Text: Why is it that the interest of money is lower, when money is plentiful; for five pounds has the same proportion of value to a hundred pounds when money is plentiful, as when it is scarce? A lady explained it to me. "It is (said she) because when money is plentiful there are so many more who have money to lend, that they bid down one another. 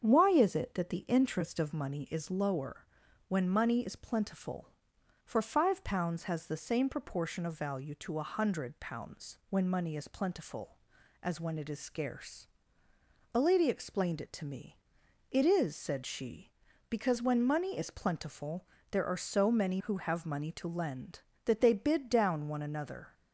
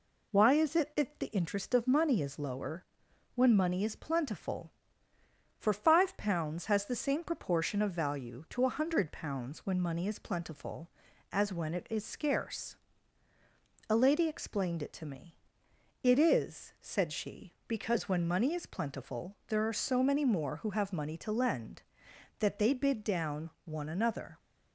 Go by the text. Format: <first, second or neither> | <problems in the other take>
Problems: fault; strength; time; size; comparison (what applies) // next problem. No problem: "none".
second | starts louder than the rest; strong; until 1.0 s; 7 dB // pauses between "plentiful" and "there"; slight; at 18.6 s; 0.24 s long // skips "more"; at 19.8 s